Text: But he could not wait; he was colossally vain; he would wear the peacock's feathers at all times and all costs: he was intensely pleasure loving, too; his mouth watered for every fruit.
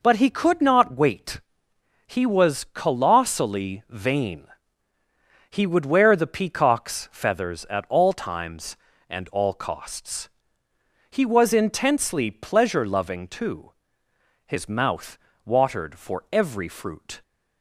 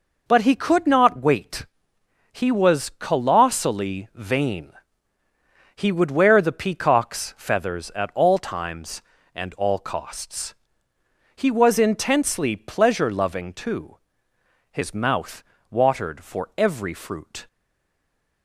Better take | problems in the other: first | pauses between "mouth" and "watered"; slight; at 15.4 s; 0.28 s long; slight in the first // stays silent after the last word; from 17.4 s on; 1.0 s long

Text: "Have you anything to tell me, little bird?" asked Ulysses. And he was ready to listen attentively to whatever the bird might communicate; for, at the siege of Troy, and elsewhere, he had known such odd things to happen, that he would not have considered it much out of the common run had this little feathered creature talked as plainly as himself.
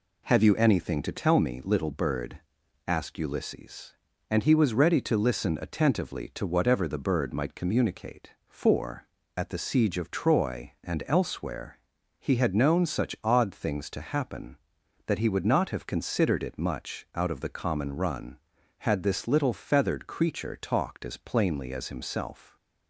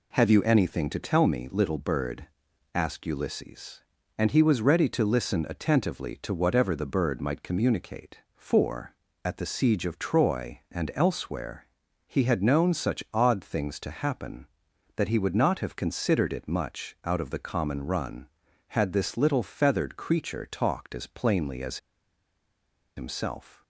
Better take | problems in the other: first | pauses between "as" and "himself"; at 21.7 s; 1.1 s long

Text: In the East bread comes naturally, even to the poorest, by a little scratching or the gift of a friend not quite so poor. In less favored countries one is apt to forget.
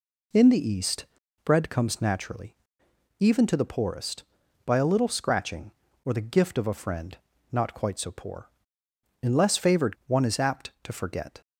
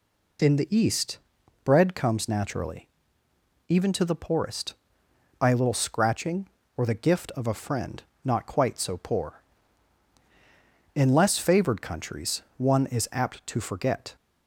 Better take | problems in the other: second | pauses between "East" and "bread"; slight; at 1.0 s; 0.36 s long; noticeable in the second // pauses between "friend" and "not"; slight; at 7.1 s; 0.34 s long; slight in the second // skips "countries"; at 10.0 s

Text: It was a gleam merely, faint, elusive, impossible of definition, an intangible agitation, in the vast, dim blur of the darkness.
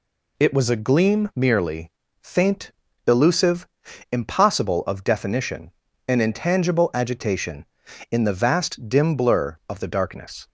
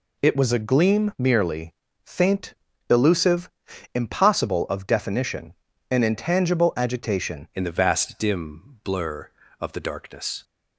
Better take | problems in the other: first | changes voice at "in"; from 7.5 s on; 2.9 s long

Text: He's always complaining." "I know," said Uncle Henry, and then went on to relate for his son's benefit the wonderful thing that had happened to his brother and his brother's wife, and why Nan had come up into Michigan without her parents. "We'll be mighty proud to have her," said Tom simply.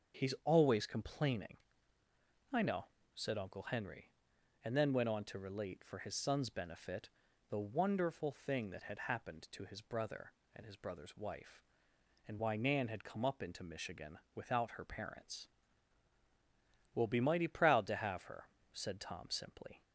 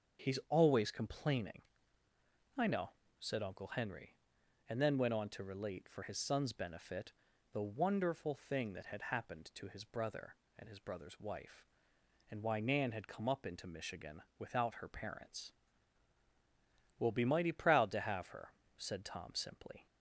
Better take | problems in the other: neither | starts louder than the rest; the same in both // pauses between "benefit" and "the"; the same in both // pauses between "Michigan" and "without"; slight; the same in both

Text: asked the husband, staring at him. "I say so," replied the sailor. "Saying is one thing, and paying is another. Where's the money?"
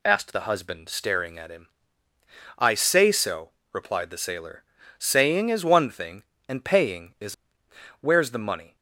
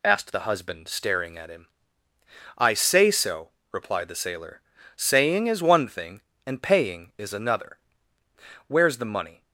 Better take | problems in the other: second | skips "another"; at 7.6 s

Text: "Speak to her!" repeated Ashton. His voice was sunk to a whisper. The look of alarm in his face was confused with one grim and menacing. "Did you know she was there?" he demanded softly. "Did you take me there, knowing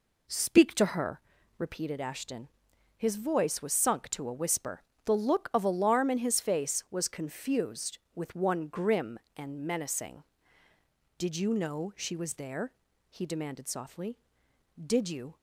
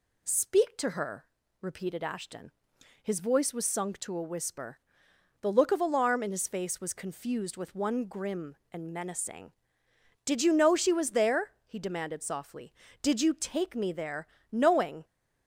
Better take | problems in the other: second | stops before "take me there knowing"; at 15.3 s

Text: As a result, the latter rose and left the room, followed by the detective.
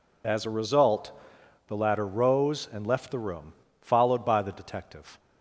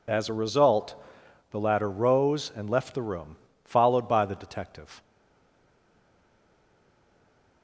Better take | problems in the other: first | stays silent after the last word; strong; from 5.0 s on; 2.6 s long

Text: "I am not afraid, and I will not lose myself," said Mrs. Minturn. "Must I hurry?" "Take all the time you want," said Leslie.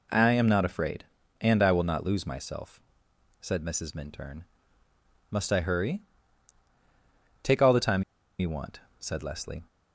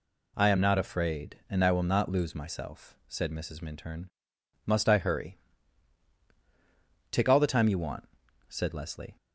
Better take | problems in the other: second | pauses between "time" and "you"; at 8.0 s; 0.37 s long

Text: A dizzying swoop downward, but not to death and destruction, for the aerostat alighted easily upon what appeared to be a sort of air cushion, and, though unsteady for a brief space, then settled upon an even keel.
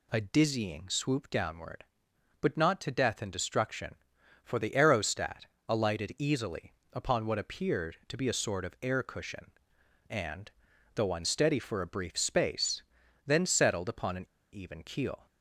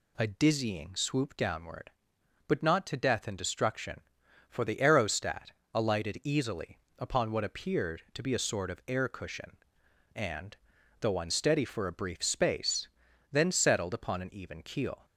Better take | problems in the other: second | pauses between "aerostat" and "alighted"; slight; at 5.4 s; 0.22 s long; slight in the second // pauses between "easily" and "upon"; slight; at 6.7 s; 0.20 s long; slight in the second // pauses between "an" and "even"; slight; at 14.2 s; 0.26 s long

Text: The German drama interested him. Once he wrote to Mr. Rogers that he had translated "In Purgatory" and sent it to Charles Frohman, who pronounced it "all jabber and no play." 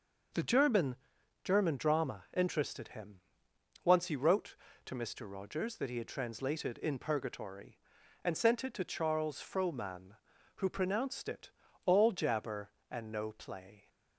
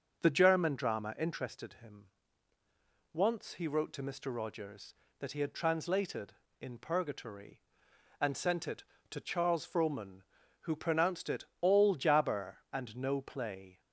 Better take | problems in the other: second | says "German" twice; at 1.4 s // pauses between "it" and "all"; slight; at 11.5 s; 0.34 s long; slight in the second

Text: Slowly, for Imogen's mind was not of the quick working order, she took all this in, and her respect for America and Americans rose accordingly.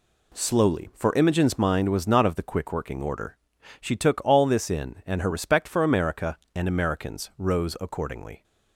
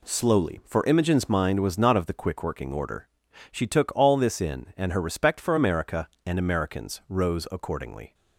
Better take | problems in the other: neither | none

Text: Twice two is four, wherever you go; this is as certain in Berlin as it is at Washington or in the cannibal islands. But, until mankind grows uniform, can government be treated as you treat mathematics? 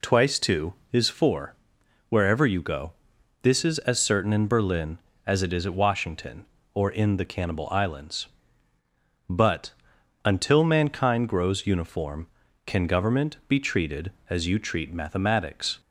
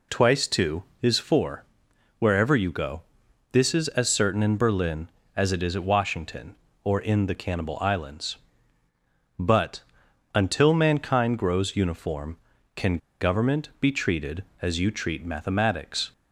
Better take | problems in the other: first | pauses between "can" and "government"; slight; at 12.9 s; 0.23 s long

